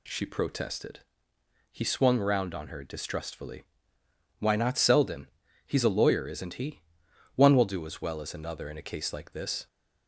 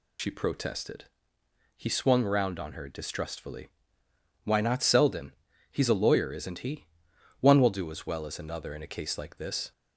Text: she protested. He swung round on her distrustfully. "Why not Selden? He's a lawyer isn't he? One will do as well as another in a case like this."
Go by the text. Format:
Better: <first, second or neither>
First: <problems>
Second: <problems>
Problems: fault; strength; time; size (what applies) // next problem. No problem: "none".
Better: first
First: none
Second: loses the start of "she"; at 0.1 s; 90 ms